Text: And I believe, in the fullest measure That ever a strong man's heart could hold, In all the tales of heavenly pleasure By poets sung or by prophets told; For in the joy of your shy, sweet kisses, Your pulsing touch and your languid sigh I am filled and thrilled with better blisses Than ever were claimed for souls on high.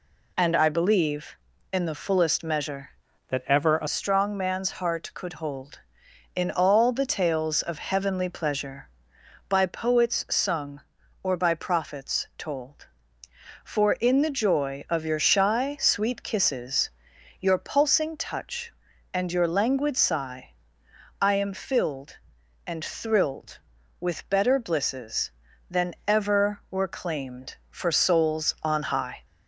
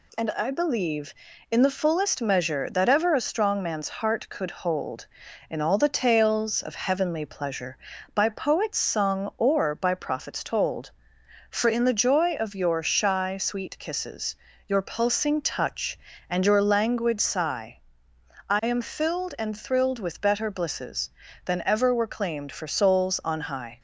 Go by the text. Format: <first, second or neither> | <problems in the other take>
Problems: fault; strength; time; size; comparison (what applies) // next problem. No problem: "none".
second | changes voice from "That" to "a"; from 3.2 to 3.8 s; 0.6 s long // pauses between "sigh" and "I"; noticeable; at 20.5 s; 0.66 s long; noticeable in the second